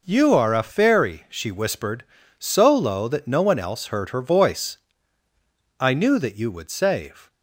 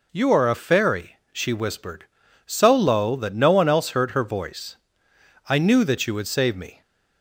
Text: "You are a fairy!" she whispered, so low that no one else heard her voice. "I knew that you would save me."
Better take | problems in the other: second | stops before "me"; at 7.2 s

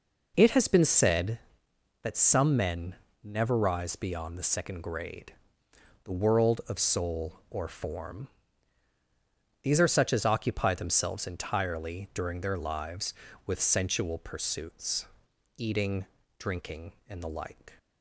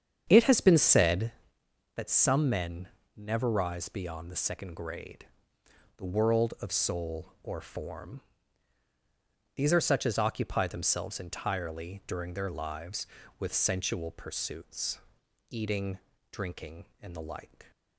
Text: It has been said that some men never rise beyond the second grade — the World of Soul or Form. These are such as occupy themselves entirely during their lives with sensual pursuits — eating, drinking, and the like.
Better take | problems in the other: first | starts louder than the rest; strong; until 1.5 s; 8 dB // pauses between "men" and "never"; slight; at 2.8 s; 0.28 s long; slight in the first

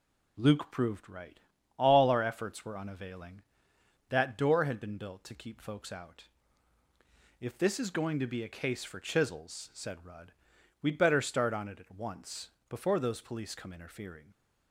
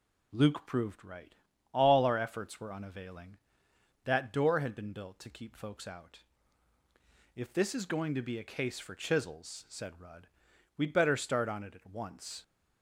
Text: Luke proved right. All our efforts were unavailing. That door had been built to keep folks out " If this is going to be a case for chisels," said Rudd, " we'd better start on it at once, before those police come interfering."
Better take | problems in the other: first | stops before "before those police come interfering"; at 12.4 s

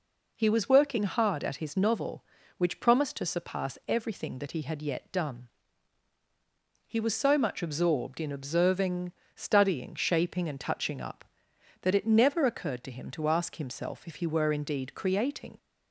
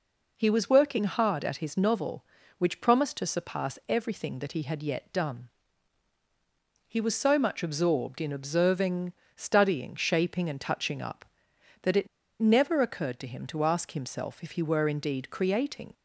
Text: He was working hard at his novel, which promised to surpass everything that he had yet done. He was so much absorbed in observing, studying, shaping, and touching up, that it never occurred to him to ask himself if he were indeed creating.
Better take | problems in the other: first | pauses between "it" and "never"; slight; at 12.0 s; 0.33 s long

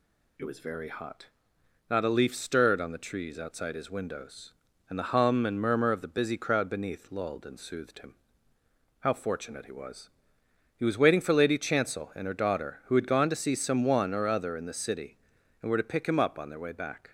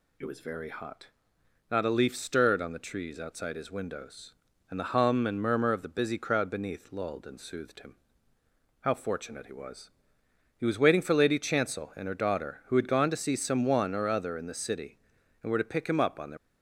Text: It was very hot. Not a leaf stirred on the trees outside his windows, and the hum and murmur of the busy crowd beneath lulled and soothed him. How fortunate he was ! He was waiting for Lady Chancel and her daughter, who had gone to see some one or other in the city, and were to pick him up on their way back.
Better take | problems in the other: first | stops before "way back"; at 16.3 s

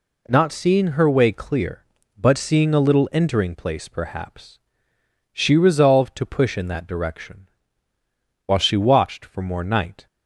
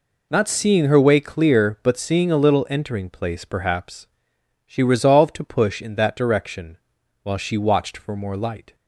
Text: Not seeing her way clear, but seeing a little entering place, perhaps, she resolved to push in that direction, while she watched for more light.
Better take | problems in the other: second | says "night" for "light"; at 9.6 s

